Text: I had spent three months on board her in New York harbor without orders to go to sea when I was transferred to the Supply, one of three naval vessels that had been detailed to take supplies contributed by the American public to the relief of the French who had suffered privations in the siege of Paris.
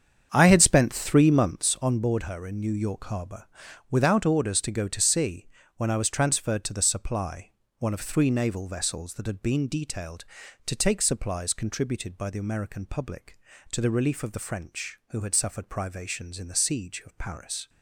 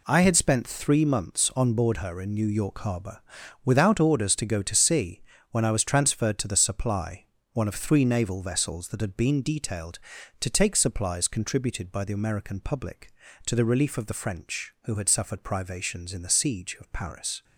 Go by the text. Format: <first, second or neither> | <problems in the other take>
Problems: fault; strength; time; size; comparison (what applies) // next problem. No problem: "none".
second | starts louder than the rest; strong; until 1.7 s; 7.5 dB // pauses between "harbor" and "without"; at 3.4 s; 0.42 s long; also in the second // pauses between "sea" and "when"; slight; at 5.4 s; 0.30 s long; slight in the second